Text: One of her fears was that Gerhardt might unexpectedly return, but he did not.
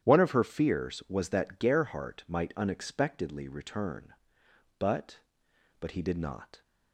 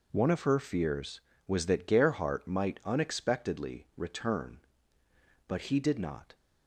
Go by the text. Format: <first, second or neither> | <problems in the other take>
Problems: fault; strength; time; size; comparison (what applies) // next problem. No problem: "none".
second | starts louder than the rest; strong; until 1.0 s; 10.5 dB // says "but" twice; at 5.7 s